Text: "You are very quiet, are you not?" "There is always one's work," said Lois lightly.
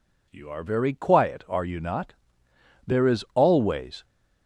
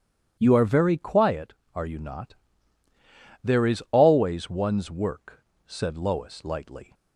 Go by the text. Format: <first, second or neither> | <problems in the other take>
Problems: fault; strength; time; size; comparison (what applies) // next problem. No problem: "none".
second | stops before "one's work said Lois lightly"; at 4.0 s